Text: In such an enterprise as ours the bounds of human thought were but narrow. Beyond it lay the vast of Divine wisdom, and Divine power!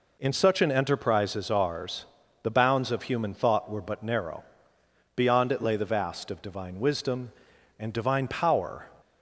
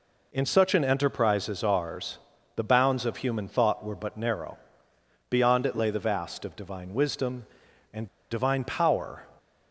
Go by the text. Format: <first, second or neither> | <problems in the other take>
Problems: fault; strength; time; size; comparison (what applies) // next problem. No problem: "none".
first | pauses between "ours" and "the"; at 2.1 s; 0.38 s long; also in the first // pauses between "and" and "Divine"; slight; at 8.0 s; 0.24 s long